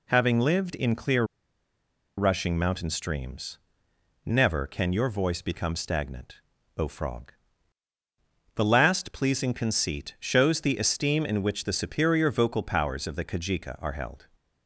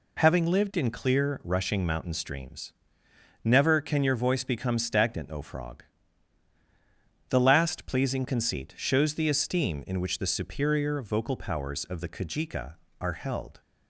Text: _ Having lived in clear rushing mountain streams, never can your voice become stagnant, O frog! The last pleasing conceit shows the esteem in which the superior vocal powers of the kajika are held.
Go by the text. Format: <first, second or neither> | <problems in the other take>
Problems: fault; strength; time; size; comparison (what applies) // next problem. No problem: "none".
second | pauses between "clear" and "rushing"; noticeable; at 1.2 s; 0.93 s long